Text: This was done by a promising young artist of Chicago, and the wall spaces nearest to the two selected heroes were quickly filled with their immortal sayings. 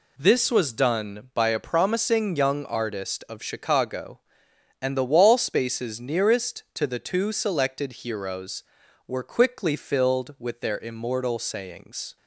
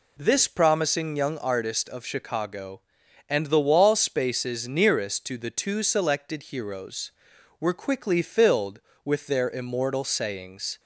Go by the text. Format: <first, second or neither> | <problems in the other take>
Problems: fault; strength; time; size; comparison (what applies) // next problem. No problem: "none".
first | skips "was done by a"; at 0.4 s